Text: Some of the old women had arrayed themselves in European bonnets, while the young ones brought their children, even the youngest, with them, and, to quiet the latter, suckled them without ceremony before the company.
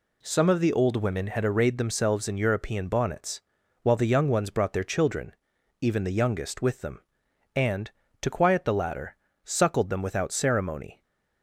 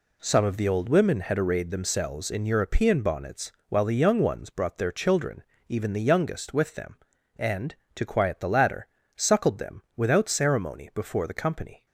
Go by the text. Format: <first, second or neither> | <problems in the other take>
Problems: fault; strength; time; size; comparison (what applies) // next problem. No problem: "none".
second | stops before "before the company"; at 11.0 s